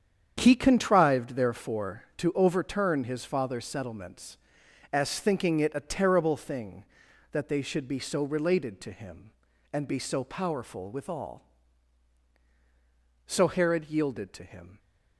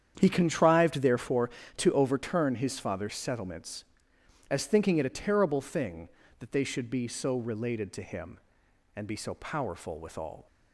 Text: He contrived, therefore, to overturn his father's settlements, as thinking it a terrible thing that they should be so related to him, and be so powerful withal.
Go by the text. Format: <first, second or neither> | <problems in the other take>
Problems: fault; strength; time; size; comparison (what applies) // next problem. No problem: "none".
second | starts louder than the rest; strong; until 1.3 s; 8 dB; strong in the second // goes on to say "So Herod yielded to him"; from 13.2 s on; 1.5 s long